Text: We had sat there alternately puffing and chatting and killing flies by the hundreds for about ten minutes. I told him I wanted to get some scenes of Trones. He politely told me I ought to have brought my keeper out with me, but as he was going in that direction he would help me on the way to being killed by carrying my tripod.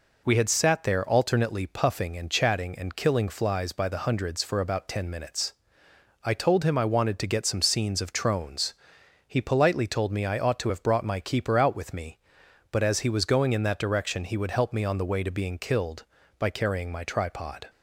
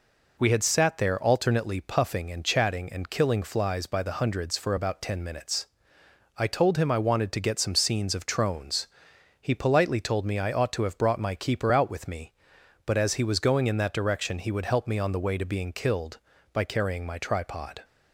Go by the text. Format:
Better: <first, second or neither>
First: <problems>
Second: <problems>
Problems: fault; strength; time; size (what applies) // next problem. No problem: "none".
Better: neither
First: none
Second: none